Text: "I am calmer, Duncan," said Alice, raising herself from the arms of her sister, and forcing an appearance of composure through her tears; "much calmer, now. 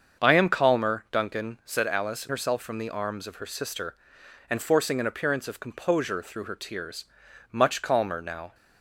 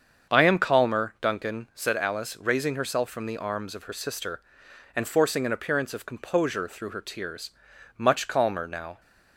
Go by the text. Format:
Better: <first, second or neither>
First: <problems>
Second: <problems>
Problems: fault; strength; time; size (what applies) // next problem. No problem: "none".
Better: second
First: starts louder than the rest; until 1.2 s; 7 dB // skips "raising"; at 2.2 s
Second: starts louder than the rest; until 1.3 s; 7 dB